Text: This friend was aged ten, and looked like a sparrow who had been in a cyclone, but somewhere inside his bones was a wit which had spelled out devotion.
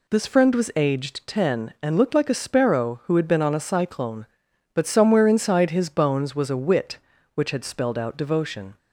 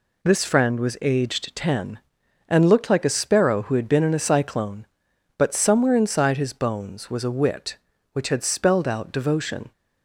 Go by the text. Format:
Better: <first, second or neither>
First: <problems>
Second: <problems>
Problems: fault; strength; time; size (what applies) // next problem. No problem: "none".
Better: second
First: says "on" for "in"; at 3.4 s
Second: none